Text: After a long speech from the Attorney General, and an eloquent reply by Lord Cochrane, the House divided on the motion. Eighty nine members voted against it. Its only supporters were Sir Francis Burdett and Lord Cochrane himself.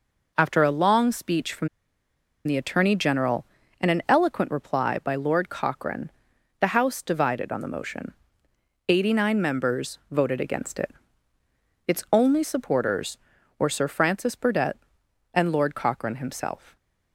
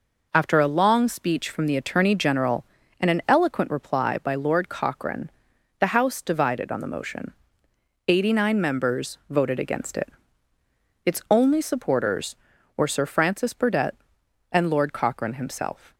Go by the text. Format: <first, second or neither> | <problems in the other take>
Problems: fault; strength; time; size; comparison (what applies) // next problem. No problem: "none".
second | pauses between "from" and "the"; noticeable; at 1.6 s; 0.77 s long